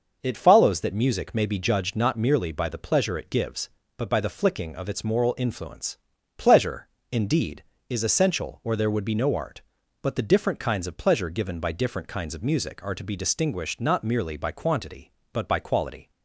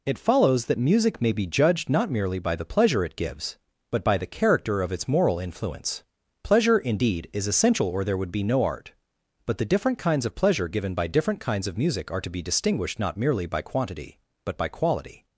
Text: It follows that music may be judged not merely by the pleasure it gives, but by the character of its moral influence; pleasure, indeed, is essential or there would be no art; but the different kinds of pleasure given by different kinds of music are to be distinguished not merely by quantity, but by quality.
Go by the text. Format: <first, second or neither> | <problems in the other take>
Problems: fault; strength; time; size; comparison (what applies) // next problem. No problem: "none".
second | says "flicking" for "character"; at 4.2 s